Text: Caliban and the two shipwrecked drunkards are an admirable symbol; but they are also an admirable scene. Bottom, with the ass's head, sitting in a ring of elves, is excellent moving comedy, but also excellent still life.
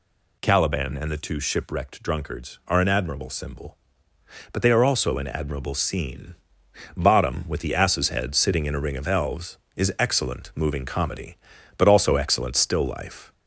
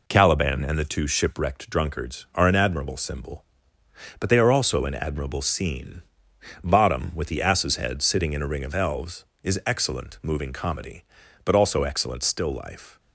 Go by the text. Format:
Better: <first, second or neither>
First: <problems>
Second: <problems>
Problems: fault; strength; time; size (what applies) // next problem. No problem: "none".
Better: second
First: gets louder; slight; throughout; 3 dB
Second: none